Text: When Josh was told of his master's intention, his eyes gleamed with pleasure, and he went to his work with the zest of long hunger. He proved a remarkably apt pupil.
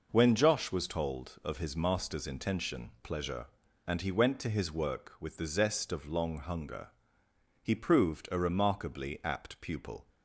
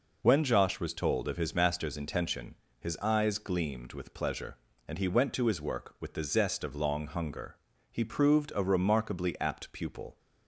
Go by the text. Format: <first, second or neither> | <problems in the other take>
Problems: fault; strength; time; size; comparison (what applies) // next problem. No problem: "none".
second | skips "his eyes gleamed with"; at 2.9 s